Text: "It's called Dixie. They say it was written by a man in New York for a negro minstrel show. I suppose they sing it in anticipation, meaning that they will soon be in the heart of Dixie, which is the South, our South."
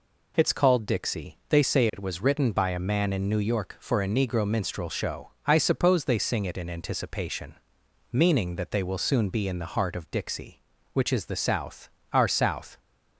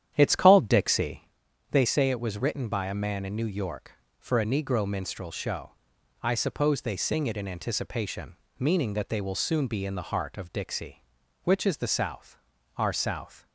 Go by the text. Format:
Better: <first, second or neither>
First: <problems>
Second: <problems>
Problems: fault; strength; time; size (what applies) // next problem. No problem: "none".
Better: first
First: none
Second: starts louder than the rest; strong; until 1.4 s; 10 dB